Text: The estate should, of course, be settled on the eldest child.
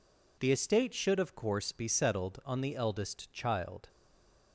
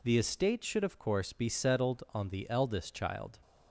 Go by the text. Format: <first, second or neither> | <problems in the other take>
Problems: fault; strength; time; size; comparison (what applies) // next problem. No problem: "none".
second | stays silent after the last word; slight; from 3.8 s on; 0.7 s long